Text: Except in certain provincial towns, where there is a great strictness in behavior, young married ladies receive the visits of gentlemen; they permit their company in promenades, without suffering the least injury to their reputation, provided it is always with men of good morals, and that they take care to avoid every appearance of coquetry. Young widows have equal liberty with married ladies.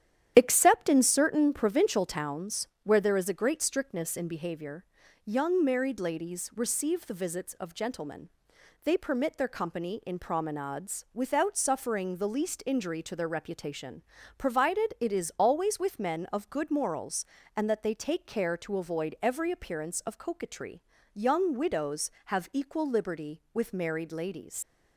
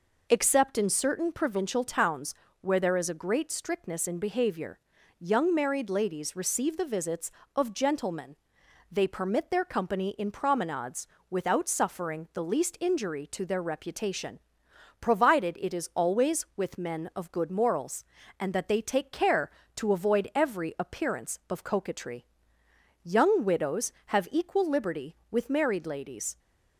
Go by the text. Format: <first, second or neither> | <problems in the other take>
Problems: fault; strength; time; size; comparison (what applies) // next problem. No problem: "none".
second | starts louder than the rest; strong; until 1.3 s; 10 dB // leaves "ladies" unfinished; at 24.6 s; 110 ms